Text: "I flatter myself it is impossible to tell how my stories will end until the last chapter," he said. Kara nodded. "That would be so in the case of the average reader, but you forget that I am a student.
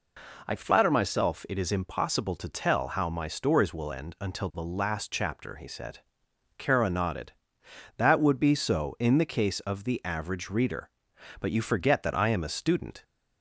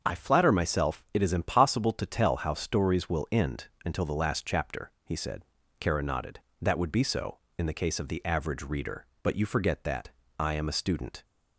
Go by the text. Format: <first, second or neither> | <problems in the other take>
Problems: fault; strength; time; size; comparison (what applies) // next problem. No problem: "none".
first | starts louder than the rest; until 1.0 s; 7 dB // skips "my"; at 2.5 s // pauses between "end" and "until"; slight; at 3.6 s; 0.18 s long // pauses between "that" and "I"; slight; at 10.0 s; 0.28 s long